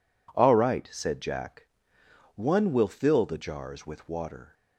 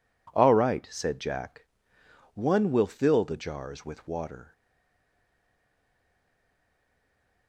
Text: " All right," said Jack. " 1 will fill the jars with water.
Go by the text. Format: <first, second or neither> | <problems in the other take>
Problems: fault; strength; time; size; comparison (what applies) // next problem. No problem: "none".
first | stays silent after the last word; strong; from 4.5 s on; 2.9 s long